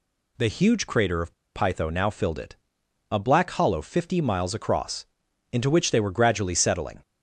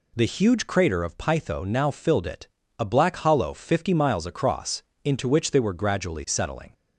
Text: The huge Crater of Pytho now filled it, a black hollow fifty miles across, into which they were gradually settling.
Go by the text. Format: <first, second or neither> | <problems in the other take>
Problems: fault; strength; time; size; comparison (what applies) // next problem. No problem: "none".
second | pauses between "of" and "Pytho"; slight; at 1.3 s; 0.23 s long